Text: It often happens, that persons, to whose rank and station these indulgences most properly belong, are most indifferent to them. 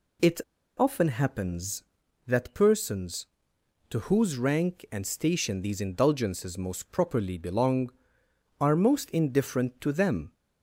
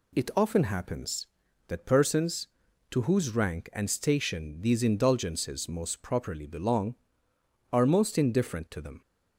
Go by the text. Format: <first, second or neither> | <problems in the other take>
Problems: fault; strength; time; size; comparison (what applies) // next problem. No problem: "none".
second | pauses between "It" and "often"; at 0.3 s; 0.38 s long